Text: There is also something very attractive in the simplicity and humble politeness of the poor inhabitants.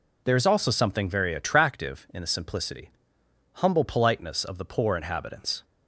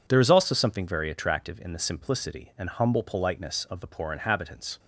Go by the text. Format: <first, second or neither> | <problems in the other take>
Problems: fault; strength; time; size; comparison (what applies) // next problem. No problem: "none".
second | skips "and"; at 3.2 s